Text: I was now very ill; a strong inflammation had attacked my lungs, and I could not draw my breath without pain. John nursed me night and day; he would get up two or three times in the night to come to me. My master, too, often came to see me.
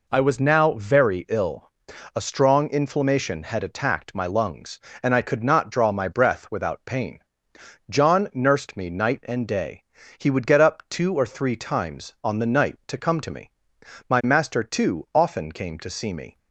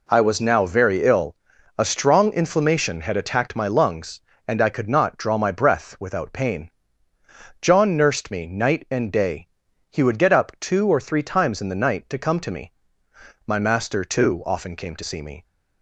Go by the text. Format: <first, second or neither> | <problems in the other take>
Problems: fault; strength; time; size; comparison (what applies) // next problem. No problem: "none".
second | says "on" for "in"; at 12.2 s